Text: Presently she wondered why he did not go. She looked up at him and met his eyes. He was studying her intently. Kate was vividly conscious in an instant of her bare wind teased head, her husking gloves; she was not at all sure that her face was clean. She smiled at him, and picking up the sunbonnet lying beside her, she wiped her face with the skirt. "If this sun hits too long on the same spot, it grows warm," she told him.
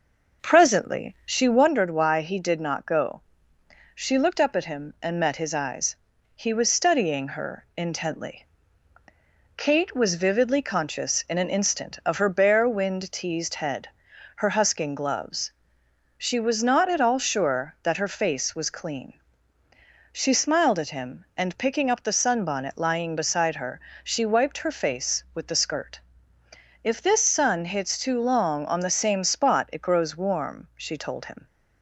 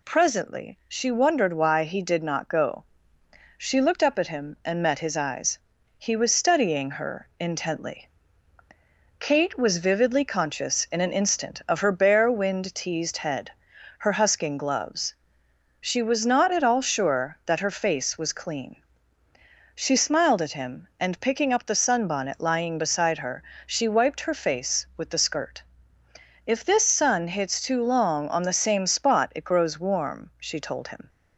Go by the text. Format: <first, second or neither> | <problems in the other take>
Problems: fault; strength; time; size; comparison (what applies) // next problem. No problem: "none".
second | starts louder than the rest; noticeable; until 1.8 s; 5.5 dB